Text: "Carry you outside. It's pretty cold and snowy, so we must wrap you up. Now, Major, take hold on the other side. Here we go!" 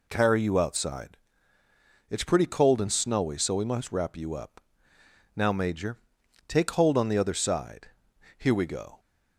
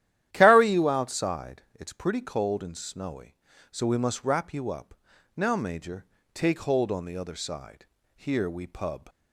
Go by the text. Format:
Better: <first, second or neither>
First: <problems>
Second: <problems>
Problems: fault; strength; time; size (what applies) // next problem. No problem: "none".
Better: first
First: none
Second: starts louder than the rest; strong; until 1.3 s; 12 dB // says "pub" for "go"; at 8.6 s